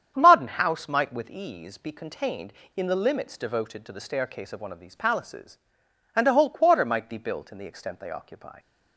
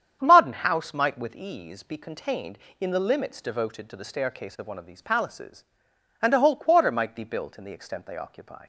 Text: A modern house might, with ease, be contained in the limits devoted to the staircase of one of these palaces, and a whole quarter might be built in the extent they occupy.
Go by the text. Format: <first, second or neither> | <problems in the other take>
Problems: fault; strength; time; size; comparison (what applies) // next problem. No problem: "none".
neither | starts louder than the rest; strong; the same in both